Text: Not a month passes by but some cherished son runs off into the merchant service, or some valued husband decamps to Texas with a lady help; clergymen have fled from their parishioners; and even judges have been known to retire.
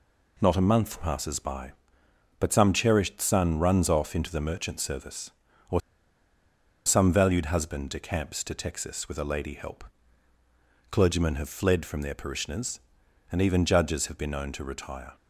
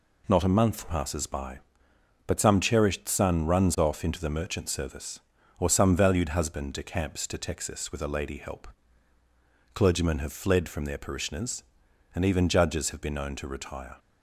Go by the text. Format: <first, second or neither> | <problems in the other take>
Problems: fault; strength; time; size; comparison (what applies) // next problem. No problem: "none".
second | pauses between "or" and "some"; at 5.7 s; 1.0 s long